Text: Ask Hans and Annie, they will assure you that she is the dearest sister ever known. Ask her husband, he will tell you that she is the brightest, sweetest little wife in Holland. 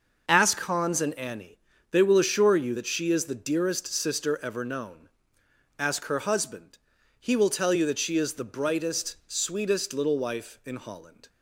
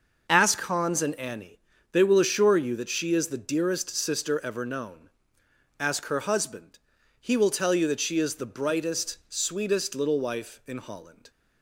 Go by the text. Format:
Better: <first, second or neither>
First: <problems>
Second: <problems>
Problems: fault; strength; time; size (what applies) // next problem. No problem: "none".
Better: neither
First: none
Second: none